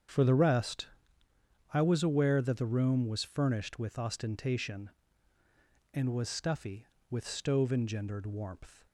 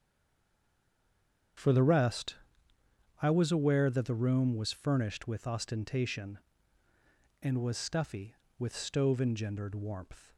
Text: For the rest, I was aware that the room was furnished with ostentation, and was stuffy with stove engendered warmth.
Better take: first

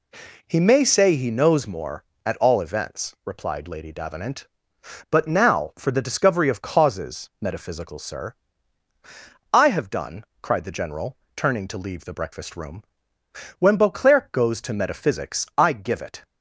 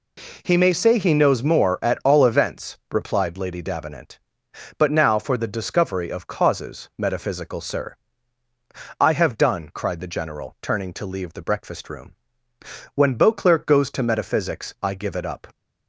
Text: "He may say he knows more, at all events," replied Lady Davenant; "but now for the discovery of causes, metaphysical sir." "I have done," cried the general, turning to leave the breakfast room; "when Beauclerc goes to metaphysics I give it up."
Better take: second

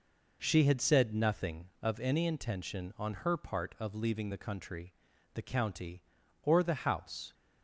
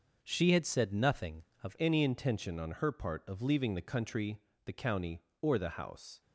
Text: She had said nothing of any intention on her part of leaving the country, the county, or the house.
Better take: first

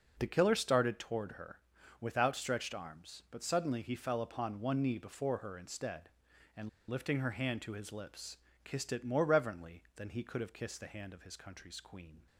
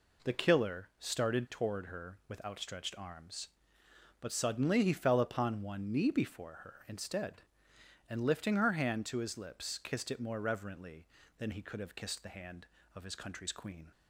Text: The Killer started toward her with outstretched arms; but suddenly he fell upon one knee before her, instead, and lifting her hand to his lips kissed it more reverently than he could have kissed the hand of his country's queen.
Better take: second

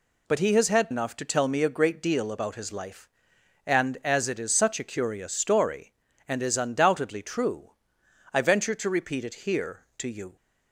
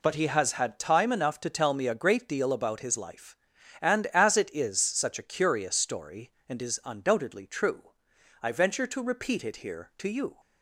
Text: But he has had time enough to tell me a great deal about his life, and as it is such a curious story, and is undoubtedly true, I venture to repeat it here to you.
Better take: second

